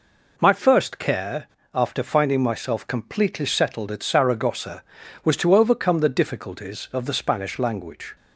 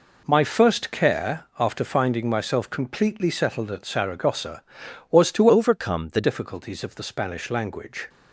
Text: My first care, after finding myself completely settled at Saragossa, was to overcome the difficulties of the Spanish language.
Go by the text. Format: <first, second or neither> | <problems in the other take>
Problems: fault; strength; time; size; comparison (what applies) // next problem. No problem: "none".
first | changes voice from "overcome" to "the"; from 5.4 to 6.2 s; 0.8 s long